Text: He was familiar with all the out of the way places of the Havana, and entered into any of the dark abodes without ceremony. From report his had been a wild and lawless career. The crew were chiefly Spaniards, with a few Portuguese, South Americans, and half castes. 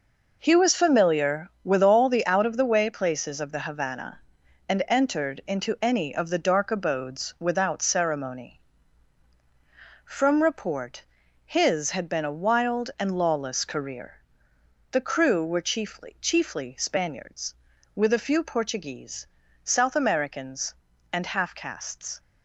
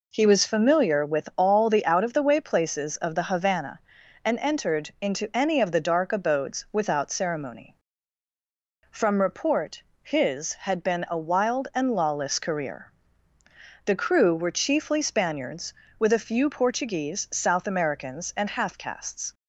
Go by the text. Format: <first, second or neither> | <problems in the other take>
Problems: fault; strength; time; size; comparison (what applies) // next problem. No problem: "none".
second | pauses between "report" and "his"; at 11.0 s; 0.40 s long; slight in the second // says "chiefly" twice; at 16.1 s